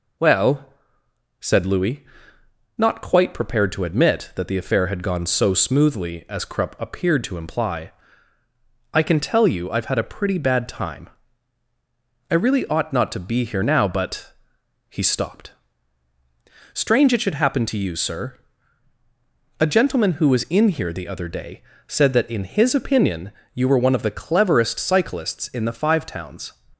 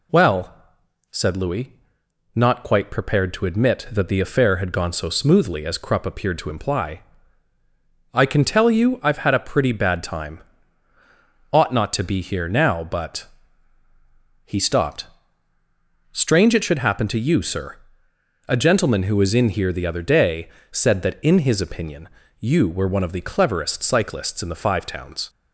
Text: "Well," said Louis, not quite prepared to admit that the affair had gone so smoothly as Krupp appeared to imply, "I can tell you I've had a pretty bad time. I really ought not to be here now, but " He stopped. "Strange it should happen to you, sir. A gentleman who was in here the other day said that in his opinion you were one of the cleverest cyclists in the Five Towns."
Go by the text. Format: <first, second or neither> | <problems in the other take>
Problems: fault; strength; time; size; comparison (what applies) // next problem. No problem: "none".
first | skips "I really"; at 10.9 s // pauses between "day" and "said"; slight; at 20.4 s; 0.22 s long; slight in the first // pauses between "opinion" and "you"; slight; at 22.0 s; 0.30 s long; slight in the first